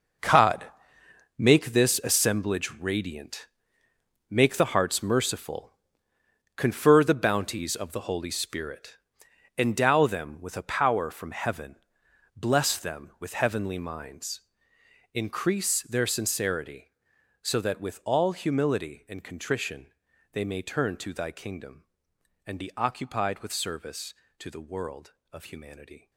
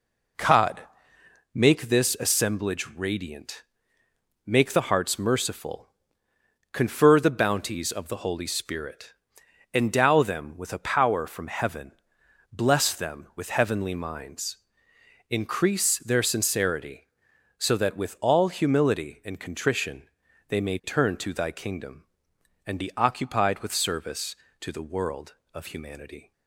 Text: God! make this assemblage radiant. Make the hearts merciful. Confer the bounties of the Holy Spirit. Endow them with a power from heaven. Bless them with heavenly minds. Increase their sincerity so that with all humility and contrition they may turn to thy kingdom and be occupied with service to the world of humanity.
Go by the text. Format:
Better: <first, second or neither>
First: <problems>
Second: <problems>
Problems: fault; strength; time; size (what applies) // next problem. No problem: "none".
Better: second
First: gets quieter; strong; throughout; 12.5 dB // pauses between "contrition" and "they"; at 19.9 s; 0.42 s long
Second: pauses between "contrition" and "they"; at 20.0 s; 0.42 s long